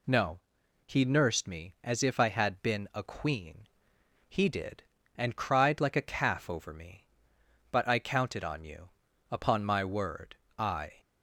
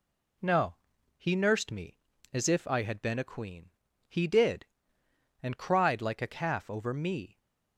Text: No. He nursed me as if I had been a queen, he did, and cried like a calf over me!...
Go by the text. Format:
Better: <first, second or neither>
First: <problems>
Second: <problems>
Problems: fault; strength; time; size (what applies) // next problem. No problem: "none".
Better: second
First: goes on to say "But I counted on you upon my word I"; strong; from 7.7 s on; 3.2 s long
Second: none